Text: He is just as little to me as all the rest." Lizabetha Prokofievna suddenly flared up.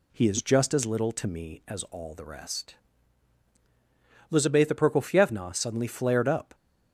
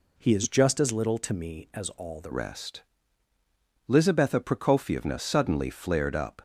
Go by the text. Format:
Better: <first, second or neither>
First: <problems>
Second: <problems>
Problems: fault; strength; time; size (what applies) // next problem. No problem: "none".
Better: first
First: none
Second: changes voice at "rest"; from 2.3 s on; 4.1 s long